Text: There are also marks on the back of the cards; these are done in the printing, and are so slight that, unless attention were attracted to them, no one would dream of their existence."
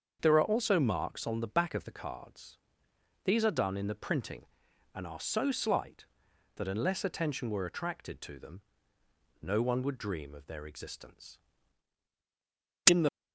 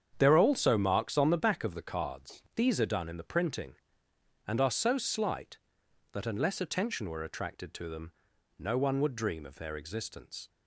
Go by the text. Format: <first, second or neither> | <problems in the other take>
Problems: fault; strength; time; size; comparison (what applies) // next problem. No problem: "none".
second | starts louder than the rest; until 1.2 s; 7 dB; strong in the second // goes on to say "In the"; slight; from 12.8 s on; 0.24 s long